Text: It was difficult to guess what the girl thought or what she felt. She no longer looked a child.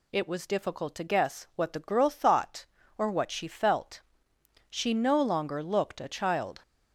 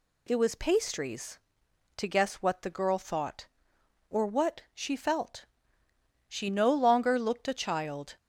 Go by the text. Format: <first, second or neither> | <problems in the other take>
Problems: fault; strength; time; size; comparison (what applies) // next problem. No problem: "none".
first | says "pastries" for "difficult"; at 0.5 s